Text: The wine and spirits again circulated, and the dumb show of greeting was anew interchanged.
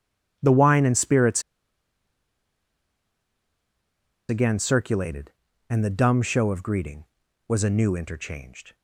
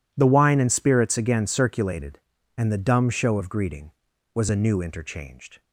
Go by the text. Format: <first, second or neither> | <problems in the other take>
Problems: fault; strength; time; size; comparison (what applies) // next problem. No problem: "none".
second | pauses between "spirits" and "again"; strong; at 1.4 s; 2.8 s long